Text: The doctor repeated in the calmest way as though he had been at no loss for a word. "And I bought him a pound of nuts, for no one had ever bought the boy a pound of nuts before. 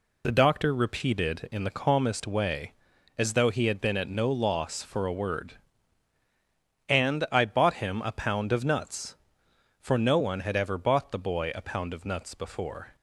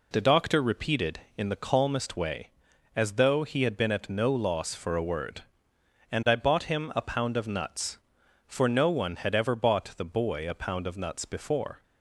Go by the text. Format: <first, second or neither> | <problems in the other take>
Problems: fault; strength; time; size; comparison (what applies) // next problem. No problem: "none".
neither | none